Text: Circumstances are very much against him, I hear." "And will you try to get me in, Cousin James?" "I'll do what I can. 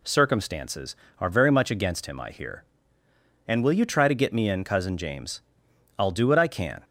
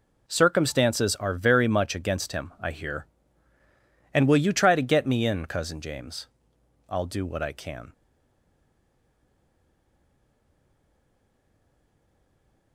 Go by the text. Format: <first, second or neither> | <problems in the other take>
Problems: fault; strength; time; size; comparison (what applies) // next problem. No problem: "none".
first | stays silent after the last word; strong; from 7.9 s on; 4.8 s long